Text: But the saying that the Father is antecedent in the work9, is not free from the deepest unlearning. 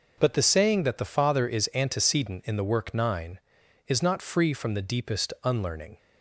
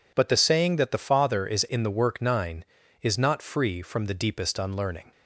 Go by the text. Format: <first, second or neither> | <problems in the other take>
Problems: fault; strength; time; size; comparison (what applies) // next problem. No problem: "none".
first | skips "antecedent"; at 1.6 s